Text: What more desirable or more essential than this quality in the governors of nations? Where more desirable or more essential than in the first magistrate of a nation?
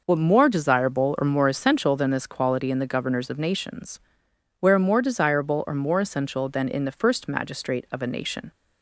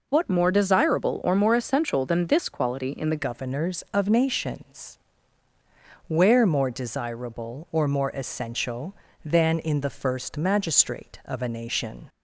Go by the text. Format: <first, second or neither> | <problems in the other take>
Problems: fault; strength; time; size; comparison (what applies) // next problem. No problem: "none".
first | changes voice at "governors"; from 3.1 s on; 8.9 s long